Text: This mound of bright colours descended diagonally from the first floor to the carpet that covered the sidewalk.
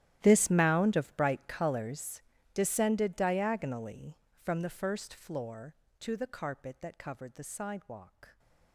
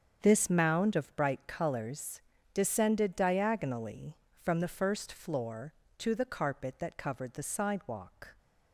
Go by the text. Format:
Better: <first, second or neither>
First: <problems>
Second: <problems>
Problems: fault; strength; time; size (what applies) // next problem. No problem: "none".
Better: second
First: gets quieter; strong; throughout; 20.5 dB // starts louder than the rest; strong; until 1.2 s; 12.5 dB // pauses between "colours" and "descended"; slight; at 2.2 s; 0.30 s long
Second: starts louder than the rest; strong; until 1.2 s; 7 dB // pauses between "colours" and "descended"; slight; at 2.2 s; 0.30 s long